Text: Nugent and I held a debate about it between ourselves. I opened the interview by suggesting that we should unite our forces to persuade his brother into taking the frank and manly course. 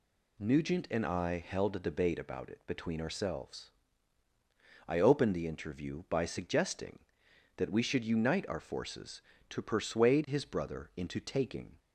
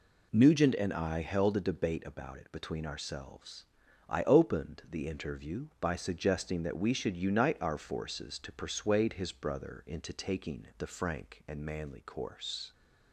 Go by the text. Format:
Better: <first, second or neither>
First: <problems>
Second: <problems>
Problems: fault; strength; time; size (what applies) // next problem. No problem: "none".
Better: second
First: stops before "the frank and manly course"; at 11.7 s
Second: none